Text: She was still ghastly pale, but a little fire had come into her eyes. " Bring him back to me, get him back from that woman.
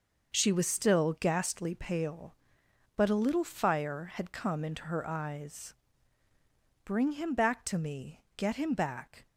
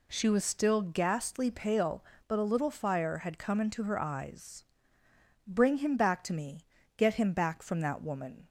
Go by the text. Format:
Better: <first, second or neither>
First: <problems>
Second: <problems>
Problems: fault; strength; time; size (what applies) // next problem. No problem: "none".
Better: second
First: starts louder than the rest; until 1.4 s; 6.5 dB // stops before "from that woman"; at 9.2 s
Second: none